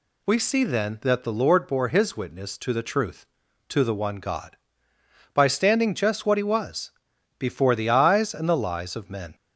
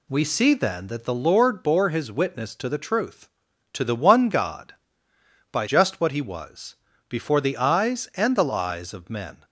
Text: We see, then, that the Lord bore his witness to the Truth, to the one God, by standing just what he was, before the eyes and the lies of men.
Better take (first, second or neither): first